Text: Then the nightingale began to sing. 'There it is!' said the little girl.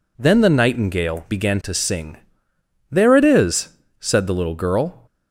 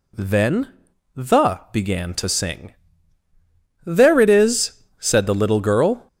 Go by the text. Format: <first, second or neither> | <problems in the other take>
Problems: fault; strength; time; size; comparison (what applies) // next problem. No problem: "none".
first | pauses between "Then" and "the"; at 0.7 s; 0.44 s long // skips "nightingale"; at 1.6 s